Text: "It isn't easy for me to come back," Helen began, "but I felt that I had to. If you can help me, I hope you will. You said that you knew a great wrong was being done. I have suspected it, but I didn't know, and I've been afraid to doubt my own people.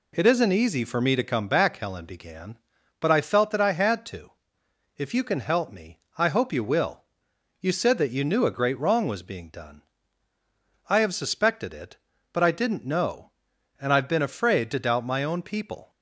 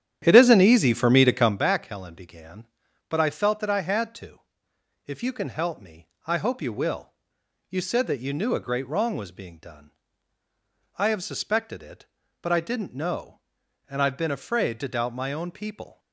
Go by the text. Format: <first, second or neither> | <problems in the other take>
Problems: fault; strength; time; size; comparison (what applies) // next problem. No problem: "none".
first | starts louder than the rest; strong; until 1.6 s; 10 dB